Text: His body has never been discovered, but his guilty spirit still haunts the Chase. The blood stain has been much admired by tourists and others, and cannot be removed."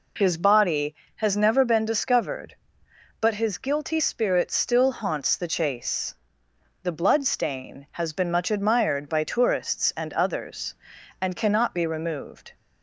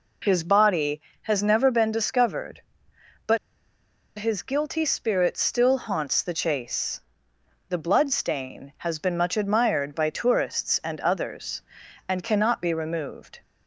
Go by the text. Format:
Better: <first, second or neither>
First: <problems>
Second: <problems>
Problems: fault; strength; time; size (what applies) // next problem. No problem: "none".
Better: first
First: none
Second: pauses between "but" and "his"; noticeable; at 3.3 s; 0.81 s long